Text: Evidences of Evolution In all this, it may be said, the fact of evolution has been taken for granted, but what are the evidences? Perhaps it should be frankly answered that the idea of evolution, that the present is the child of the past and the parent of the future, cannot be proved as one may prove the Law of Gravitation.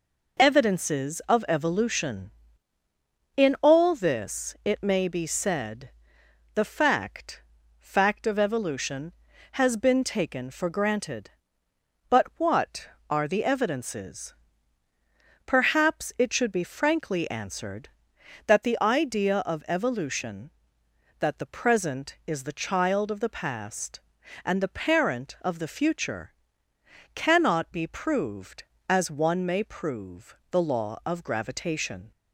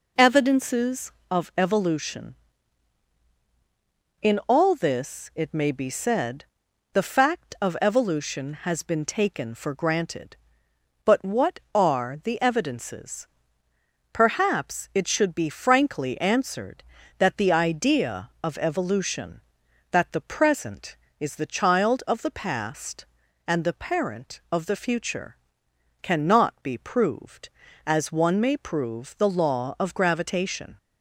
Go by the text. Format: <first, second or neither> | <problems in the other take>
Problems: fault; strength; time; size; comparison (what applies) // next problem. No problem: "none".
second | says "fact" twice; at 7.7 s // pauses between "prove" and "the"; slight; at 30.3 s; 0.16 s long